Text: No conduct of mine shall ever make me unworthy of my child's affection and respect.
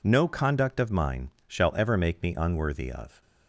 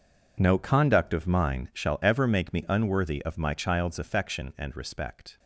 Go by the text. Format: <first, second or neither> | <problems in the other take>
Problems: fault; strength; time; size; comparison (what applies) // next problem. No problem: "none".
second | pauses between "mine" and "shall"; slight; at 1.2 s; 0.20 s long // stops before "my child's affection and respect"; at 3.2 s